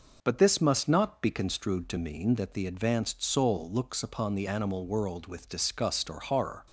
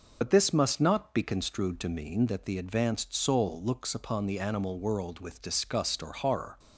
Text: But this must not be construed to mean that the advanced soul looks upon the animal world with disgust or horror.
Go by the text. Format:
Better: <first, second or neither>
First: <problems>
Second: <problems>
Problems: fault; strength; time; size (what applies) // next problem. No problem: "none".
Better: first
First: none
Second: loses the start of "But"; at 0.2 s; 70 ms